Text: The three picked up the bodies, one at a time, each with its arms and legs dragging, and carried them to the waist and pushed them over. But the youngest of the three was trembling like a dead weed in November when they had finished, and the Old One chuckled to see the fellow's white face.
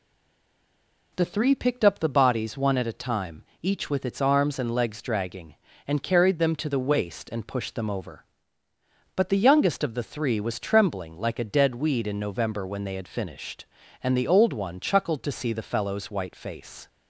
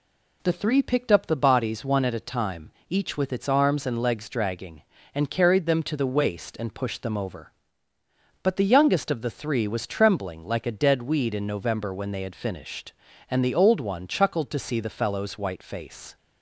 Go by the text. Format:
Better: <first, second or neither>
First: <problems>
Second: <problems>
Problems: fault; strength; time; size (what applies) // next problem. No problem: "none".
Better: second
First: stays silent before the first word; until 1.1 s; 1.1 s long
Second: none